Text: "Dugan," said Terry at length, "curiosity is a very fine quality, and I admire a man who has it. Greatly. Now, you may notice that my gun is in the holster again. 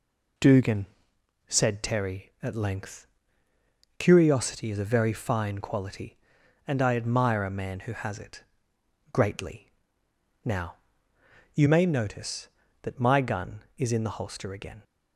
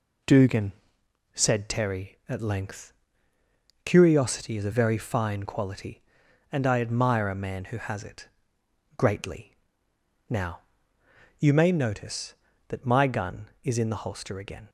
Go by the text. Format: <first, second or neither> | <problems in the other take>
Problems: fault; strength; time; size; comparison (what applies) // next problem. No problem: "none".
neither | none